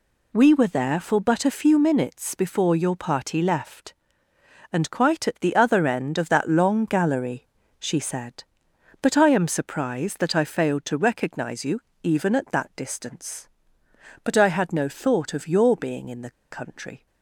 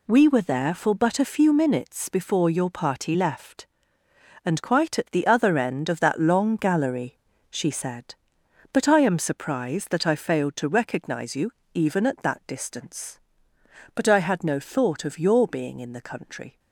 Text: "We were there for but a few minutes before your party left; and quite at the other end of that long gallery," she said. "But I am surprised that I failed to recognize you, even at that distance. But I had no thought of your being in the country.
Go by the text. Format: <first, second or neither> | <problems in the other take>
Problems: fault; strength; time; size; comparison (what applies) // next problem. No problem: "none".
second | pauses between "the" and "country"; slight; at 16.3 s; 0.20 s long